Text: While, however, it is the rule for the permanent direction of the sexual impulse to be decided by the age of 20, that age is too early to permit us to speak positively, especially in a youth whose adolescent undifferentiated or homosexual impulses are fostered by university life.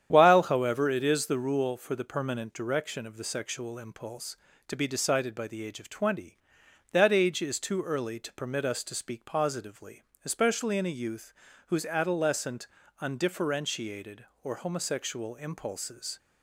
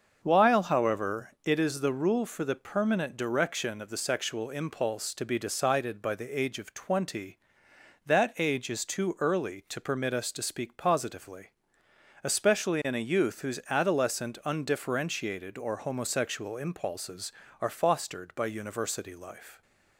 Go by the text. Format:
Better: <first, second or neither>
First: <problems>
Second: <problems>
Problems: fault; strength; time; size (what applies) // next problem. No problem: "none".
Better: second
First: starts louder than the rest; strong; until 1.1 s; 9.5 dB // pauses between "youth" and "whose"; slight; at 11.3 s; 0.36 s long // pauses between "adolescent" and "undifferentiated"; slight; at 12.6 s; 0.34 s long // stops before "are fostered by university life"; at 16.1 s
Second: starts louder than the rest; until 1.2 s; 6.5 dB